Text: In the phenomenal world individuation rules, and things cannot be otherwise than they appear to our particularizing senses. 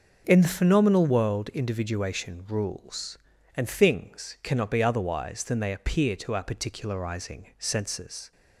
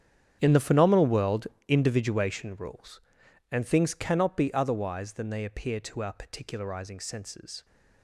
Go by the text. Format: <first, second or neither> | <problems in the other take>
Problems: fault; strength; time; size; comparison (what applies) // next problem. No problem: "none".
first | gets quieter; strong; throughout; 16 dB // starts louder than the rest; strong; until 1.4 s; 8.5 dB; noticeable in the first // pauses between "world" and "individuation"; slight; at 1.4 s; 0.18 s long